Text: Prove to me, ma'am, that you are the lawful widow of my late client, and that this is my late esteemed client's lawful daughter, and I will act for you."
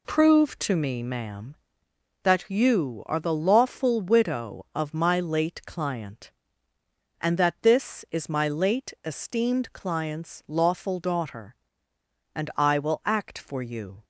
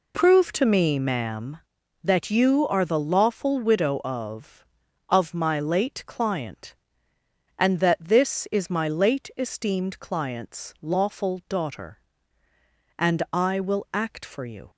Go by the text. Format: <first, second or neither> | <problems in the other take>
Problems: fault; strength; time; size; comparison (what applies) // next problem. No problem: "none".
first | says "of" twice; at 5.0 s